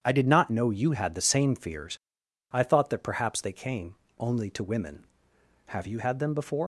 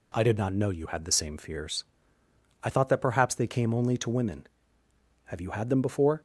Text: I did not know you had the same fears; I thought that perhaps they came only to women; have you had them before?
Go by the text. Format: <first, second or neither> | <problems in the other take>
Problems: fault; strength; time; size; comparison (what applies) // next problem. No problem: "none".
second | starts louder than the rest; strong; until 1.0 s; 8.5 dB // pauses between "came" and "only"; slight; at 3.9 s; 0.22 s long // leaves "before" unfinished; at 6.6 s; 125 ms